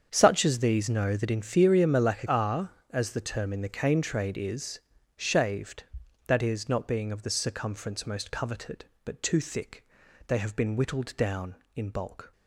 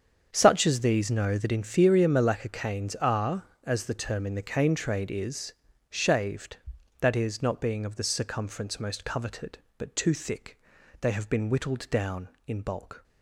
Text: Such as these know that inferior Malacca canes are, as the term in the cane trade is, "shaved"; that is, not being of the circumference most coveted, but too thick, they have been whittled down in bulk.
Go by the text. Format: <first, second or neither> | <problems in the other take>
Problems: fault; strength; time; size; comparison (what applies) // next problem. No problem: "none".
second | starts louder than the rest; strong; until 1.1 s; 7.5 dB; strong in the second // skips "canes"; at 2.2 s